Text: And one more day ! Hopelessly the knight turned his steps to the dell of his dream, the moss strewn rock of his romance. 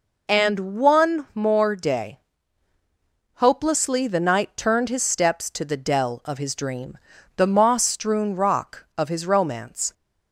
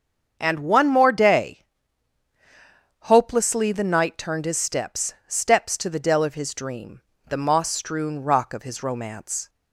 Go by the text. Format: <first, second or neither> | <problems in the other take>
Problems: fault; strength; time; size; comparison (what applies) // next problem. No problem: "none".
first | starts louder than the rest; strong; until 1.3 s; 7 dB // says "steps" twice; at 5.2 s